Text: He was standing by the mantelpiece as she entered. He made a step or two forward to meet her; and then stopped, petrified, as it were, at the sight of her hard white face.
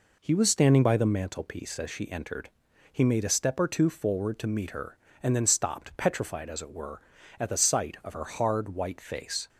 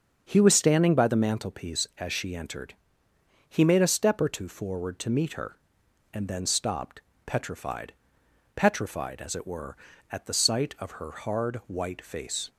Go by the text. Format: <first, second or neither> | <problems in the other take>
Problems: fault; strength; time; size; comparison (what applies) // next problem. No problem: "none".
first | starts louder than the rest; until 1.2 s; 7 dB // says "petrified" twice; at 8.5 s